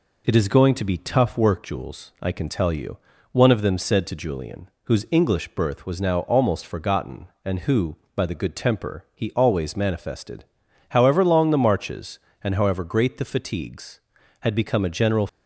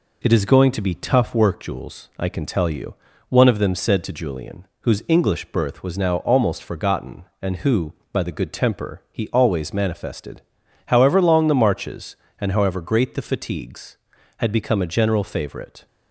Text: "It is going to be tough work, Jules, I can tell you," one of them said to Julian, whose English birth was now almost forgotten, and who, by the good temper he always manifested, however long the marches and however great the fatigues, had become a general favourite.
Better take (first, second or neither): second